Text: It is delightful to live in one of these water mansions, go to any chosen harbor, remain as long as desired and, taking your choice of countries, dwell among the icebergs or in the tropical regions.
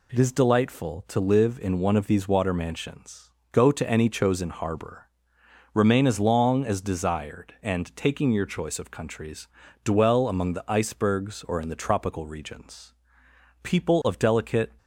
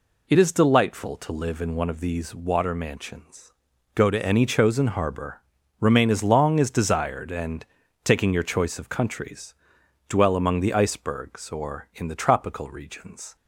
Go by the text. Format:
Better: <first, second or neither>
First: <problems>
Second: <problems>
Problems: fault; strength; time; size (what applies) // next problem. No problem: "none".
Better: second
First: goes on to say "People of delicate"; noticeable; from 13.6 s on; 1.1 s long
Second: none